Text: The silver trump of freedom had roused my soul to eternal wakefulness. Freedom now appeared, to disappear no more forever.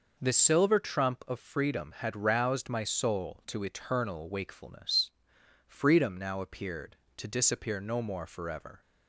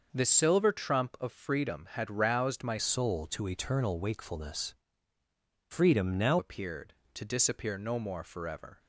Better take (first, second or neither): first